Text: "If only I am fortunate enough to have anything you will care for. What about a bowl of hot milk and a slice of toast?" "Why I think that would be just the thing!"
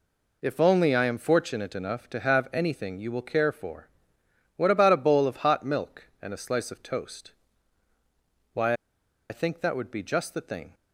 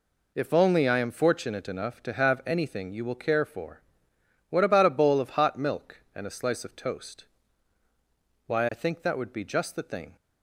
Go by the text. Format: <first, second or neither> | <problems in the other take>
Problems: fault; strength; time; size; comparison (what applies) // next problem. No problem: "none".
second | pauses between "Why" and "I"; noticeable; at 8.7 s; 0.55 s long